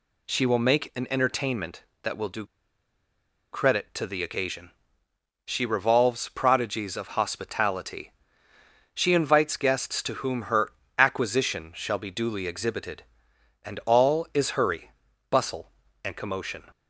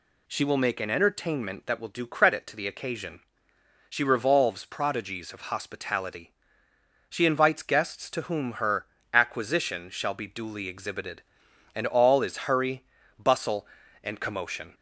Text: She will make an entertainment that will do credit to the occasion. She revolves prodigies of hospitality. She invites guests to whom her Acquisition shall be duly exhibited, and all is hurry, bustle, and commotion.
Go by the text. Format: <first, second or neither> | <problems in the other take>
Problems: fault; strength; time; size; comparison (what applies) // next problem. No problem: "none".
second | pauses between "do" and "credit"; at 2.4 s; 1.0 s long // pauses between "her" and "Acquisition"; slight; at 10.7 s; 0.26 s long; slight in the second